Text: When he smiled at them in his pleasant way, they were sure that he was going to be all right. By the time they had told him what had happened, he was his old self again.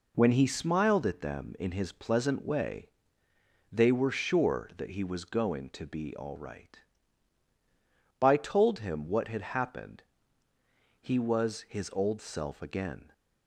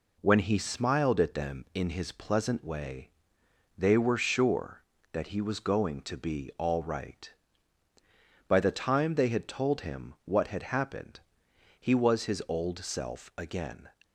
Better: second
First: skips "the time they had"; at 8.3 s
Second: none

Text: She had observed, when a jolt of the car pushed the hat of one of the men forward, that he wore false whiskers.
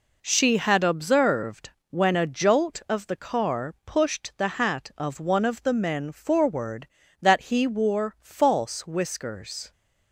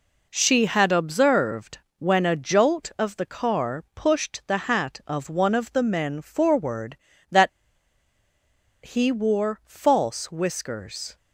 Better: first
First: none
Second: pauses between "that" and "he"; strong; at 7.4 s; 1.3 s long

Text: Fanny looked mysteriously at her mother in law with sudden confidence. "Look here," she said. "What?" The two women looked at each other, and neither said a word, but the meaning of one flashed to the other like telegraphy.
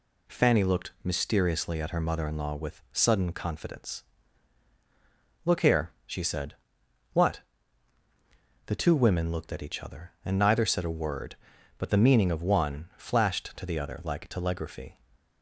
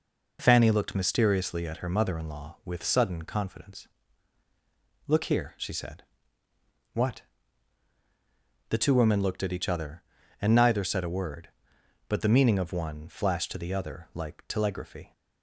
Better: neither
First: none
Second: none

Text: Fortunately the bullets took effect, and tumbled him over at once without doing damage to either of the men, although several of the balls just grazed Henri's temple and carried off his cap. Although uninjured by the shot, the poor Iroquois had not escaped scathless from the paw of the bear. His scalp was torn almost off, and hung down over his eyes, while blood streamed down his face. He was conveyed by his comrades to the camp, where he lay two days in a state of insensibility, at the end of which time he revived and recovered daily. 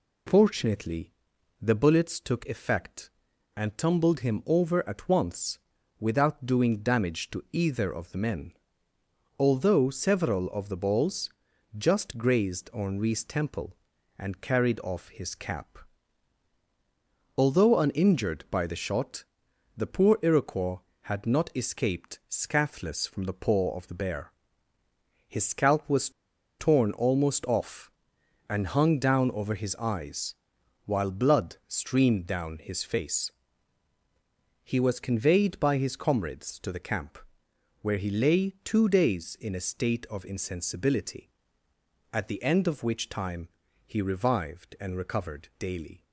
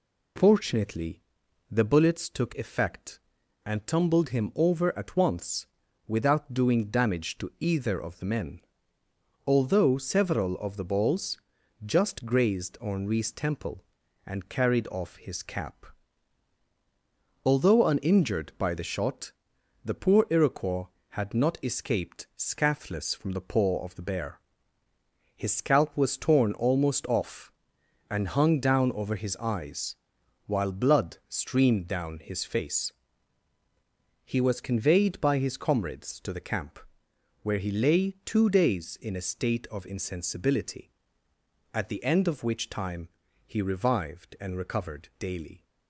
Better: second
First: pauses between "Fortunately" and "the"; noticeable; at 1.1 s; 0.48 s long // pauses between "once" and "without"; at 5.5 s; 0.42 s long // pauses between "balls" and "just"; noticeable; at 11.3 s; 0.46 s long // pauses between "was" and "torn"; noticeable; at 26.0 s; 0.49 s long // pauses between "time" and "he"; at 43.4 s; 0.38 s long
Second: pauses between "Fortunately" and "the"; noticeable; at 1.2 s; 0.48 s long // pauses between "once" and "without"; at 5.6 s; 0.42 s long // pauses between "balls" and "just"; noticeable; at 11.3 s; 0.46 s long // pauses between "time" and "he"; at 43.0 s; 0.38 s long

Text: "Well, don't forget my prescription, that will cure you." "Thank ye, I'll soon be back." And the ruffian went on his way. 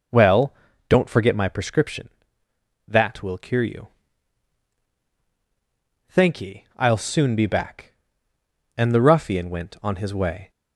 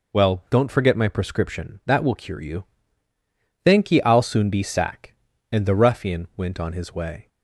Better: first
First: none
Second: says "sack" for "back"; at 4.6 s

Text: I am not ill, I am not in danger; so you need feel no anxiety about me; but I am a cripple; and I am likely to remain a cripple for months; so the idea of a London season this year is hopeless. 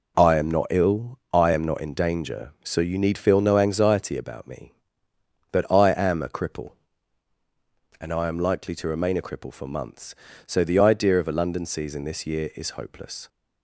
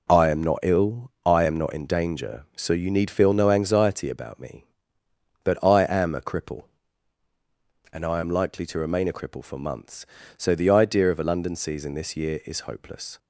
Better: neither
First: none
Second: none

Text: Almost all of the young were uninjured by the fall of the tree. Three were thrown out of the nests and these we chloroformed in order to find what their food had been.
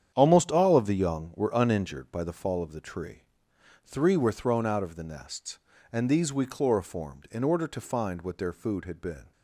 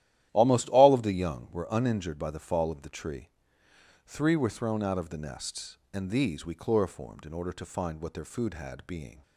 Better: first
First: starts louder than the rest; strong; until 1.1 s; 9 dB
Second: starts louder than the rest; strong; until 1.3 s; 12.5 dB // says "being" for "been"; at 8.8 s

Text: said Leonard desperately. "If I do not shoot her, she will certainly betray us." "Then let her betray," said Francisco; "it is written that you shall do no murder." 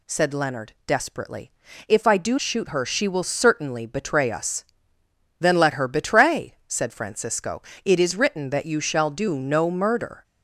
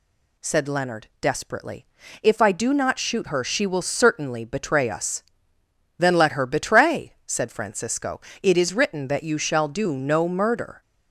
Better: second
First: skips "not"; at 2.3 s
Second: none

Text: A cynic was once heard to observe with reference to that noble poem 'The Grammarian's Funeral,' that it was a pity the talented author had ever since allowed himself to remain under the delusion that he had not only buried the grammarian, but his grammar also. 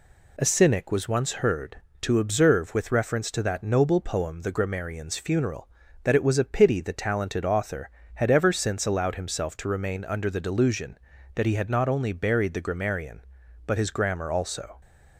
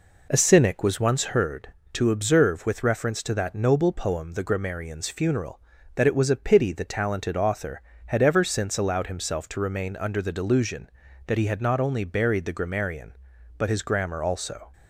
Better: first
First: none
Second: starts louder than the rest; until 1.4 s; 4 dB

